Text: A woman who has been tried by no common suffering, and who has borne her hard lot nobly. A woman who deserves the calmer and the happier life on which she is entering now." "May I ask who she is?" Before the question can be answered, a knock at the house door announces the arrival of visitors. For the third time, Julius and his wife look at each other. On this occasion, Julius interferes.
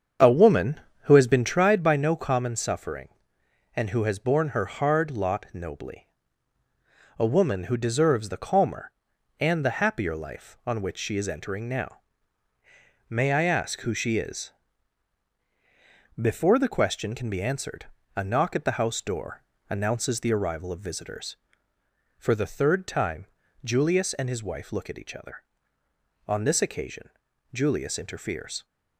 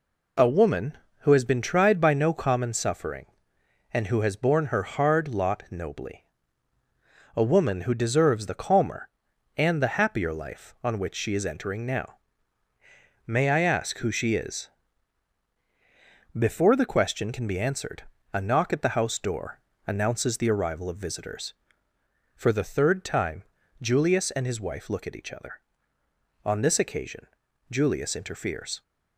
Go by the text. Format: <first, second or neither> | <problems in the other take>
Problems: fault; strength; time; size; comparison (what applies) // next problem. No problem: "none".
second | starts louder than the rest; strong; until 1.7 s; 7 dB // pauses between "door" and "announces"; slight; at 19.4 s; 0.30 s long; slight in the second